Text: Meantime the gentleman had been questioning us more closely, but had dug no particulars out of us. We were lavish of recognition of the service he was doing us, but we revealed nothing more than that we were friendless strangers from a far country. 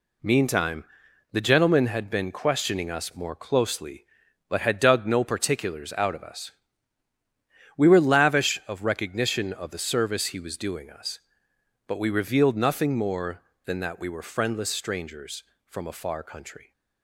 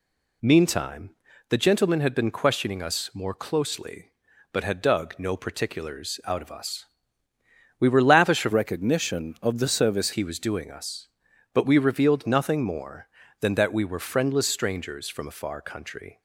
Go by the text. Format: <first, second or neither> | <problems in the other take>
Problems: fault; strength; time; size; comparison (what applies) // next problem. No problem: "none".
first | pauses between "Meantime" and "the"; at 1.0 s; 0.38 s long; noticeable in the first // changes voice from "recognition" to "service"; from 8.5 to 10.1 s; 1.6 s long